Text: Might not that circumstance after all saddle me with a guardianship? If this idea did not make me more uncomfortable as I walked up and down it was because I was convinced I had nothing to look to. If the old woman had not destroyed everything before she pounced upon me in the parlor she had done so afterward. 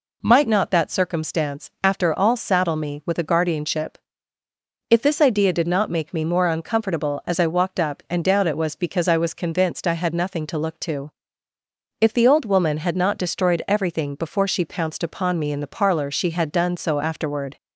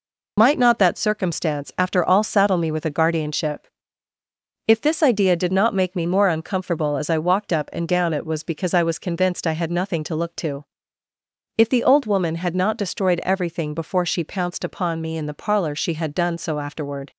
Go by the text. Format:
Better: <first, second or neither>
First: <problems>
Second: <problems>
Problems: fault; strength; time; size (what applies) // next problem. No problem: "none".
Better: first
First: none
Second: loses the start of "Might"; at 0.3 s; 60 ms